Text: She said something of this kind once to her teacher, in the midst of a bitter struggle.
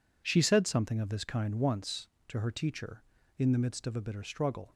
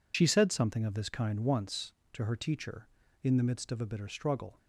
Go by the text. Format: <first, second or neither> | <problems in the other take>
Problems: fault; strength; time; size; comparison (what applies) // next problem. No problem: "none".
first | loses the start of "She"; at 0.1 s; 50 ms